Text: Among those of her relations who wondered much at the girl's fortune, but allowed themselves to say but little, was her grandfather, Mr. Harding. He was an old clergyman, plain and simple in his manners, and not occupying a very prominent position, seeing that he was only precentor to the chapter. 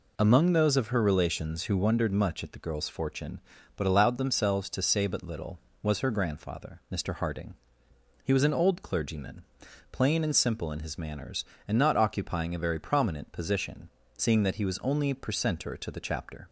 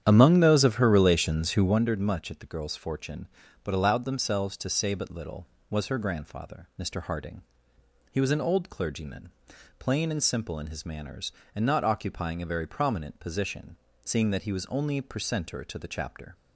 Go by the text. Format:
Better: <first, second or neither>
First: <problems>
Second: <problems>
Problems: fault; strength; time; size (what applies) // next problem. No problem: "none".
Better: first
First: none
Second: starts louder than the rest; strong; until 1.9 s; 9.5 dB